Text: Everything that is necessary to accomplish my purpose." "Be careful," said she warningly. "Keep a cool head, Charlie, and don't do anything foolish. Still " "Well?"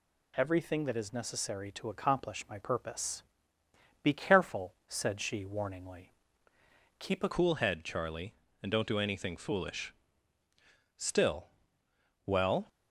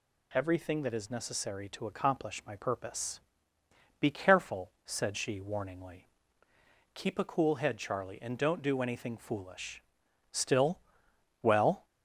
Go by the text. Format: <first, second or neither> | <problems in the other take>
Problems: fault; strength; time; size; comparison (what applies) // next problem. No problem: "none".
second | changes voice at "cool"; from 7.3 s on; 5.3 s long